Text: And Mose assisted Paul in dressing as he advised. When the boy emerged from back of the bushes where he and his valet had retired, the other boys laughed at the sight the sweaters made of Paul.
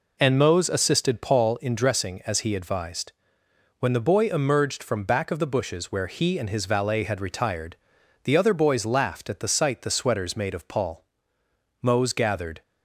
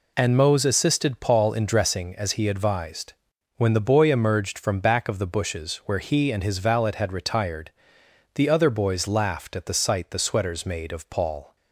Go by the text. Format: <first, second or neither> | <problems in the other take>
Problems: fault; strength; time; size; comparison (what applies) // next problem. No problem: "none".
second | goes on to say "Mose gathered"; noticeable; from 11.8 s on; 0.80 s long